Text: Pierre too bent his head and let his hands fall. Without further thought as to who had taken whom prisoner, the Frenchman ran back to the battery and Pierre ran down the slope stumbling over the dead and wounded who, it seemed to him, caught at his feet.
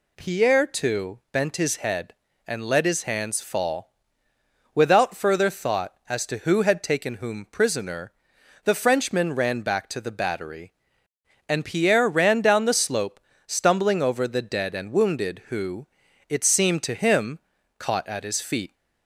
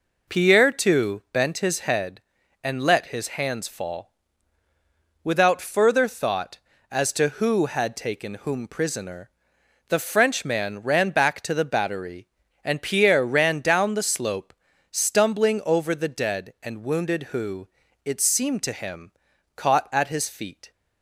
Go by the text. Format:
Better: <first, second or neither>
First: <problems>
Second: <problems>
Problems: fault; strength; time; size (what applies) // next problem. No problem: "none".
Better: neither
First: pauses between "slope" and "stumbling"; slight; at 13.1 s; 0.28 s long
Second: pauses between "slope" and "stumbling"; at 14.5 s; 0.38 s long